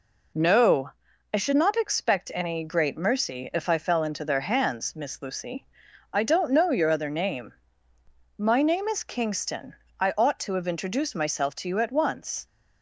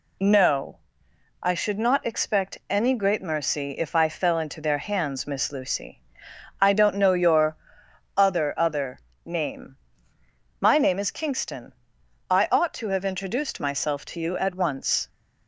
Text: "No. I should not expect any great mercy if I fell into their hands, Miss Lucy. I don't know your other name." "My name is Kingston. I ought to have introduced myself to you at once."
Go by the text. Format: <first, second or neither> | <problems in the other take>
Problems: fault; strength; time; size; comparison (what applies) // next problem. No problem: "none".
first | pauses between "your" and "other"; noticeable; at 7.5 s; 0.60 s long // says "other" twice; at 8.5 s